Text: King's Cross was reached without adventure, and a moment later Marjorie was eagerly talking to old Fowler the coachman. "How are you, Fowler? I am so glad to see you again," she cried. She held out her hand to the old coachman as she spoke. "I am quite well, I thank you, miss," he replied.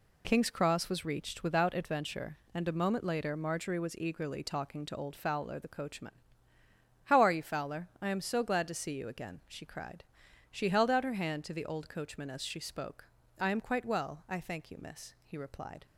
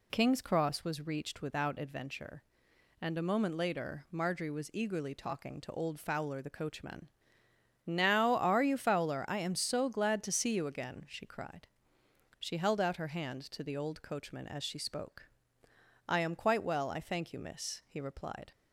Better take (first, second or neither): first